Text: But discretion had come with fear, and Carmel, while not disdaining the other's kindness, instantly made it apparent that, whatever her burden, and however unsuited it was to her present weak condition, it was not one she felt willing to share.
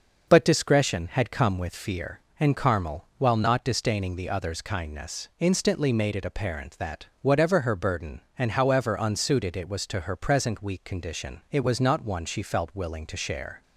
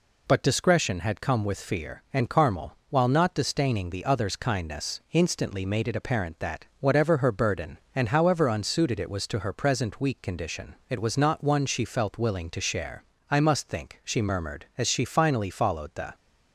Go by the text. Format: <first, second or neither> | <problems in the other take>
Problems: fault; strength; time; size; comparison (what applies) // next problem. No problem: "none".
first | goes on to say "I must think she murmured as she finally followed the"; strong; from 13.2 s on; 2.8 s long